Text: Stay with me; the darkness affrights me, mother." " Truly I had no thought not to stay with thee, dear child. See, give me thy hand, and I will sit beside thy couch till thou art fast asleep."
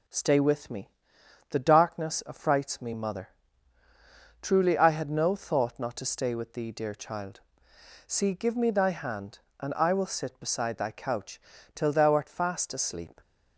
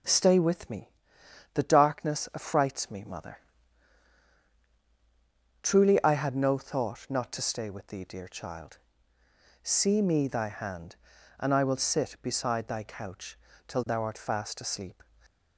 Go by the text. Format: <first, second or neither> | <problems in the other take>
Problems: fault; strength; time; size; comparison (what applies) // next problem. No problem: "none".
first | skips "give"; at 10.0 s // pauses between "couch" and "till"; slight; at 13.3 s; 0.30 s long; slight in the first